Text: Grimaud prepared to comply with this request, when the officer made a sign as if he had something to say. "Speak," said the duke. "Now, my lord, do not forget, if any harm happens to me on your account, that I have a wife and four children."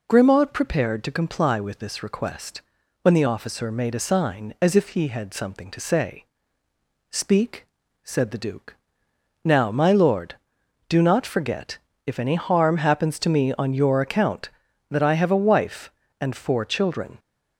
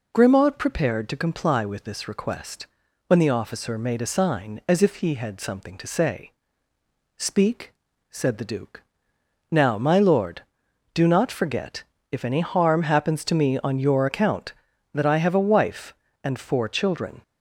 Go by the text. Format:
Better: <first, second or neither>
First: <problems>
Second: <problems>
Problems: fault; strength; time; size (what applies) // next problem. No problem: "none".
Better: neither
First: none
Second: none